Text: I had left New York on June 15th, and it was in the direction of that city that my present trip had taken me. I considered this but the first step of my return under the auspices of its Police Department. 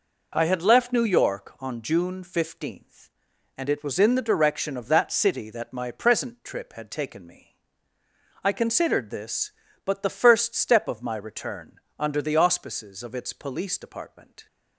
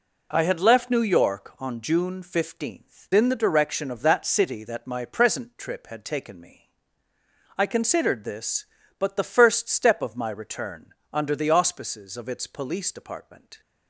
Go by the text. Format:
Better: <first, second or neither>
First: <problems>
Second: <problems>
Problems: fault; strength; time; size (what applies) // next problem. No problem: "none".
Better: first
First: pauses between "return" and "under"; slight; at 11.7 s; 0.26 s long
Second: skips "and it was"; at 3.1 s // pauses between "return" and "under"; slight; at 10.8 s; 0.26 s long